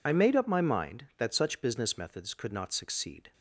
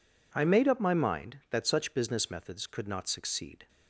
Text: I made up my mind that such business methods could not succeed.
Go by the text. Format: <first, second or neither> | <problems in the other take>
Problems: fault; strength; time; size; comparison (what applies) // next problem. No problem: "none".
second | loses the start of "I"; at 0.0 s; 50 ms